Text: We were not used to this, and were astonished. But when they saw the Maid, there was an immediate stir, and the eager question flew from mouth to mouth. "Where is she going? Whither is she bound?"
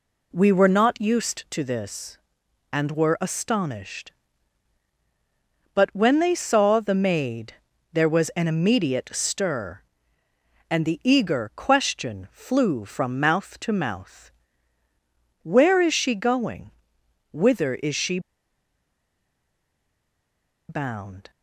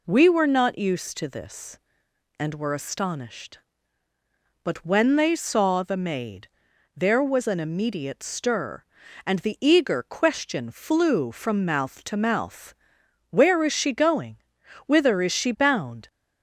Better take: second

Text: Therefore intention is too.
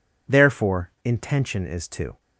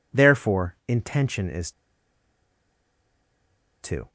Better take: first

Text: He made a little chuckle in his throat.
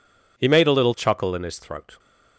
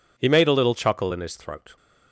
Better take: neither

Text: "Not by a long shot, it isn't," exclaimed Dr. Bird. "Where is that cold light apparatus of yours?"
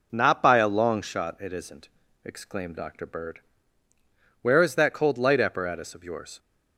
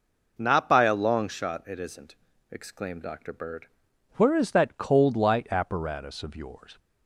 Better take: first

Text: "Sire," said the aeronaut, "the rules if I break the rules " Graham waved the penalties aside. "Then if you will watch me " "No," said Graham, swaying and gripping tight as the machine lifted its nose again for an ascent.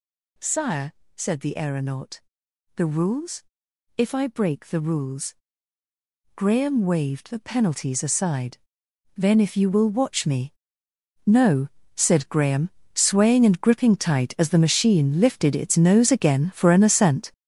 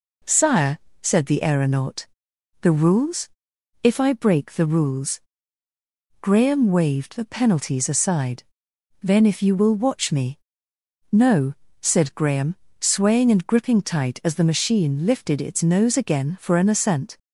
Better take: second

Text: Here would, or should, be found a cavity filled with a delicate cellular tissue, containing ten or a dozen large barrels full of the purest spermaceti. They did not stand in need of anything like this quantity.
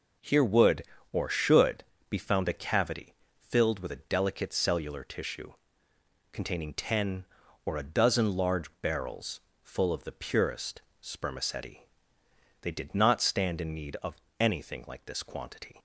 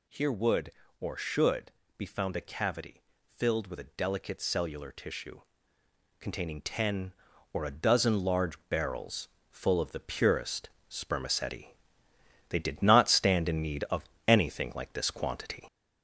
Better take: first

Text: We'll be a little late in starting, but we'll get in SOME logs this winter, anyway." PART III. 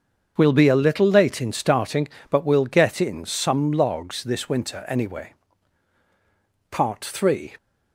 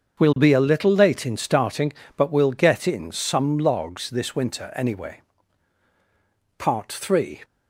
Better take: neither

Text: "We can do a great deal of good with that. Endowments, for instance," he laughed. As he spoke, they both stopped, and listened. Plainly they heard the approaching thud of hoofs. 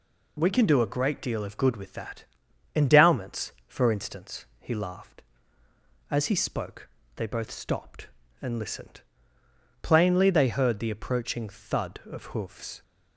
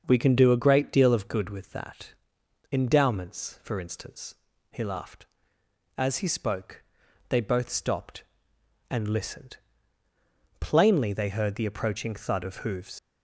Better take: first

